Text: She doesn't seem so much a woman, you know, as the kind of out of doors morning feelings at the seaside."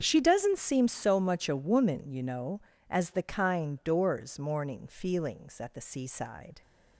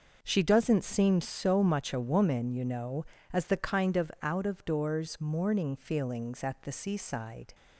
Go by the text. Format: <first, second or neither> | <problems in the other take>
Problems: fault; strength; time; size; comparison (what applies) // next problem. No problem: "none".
second | starts louder than the rest; until 1.0 s; 7 dB // skips "of out of"; at 3.8 s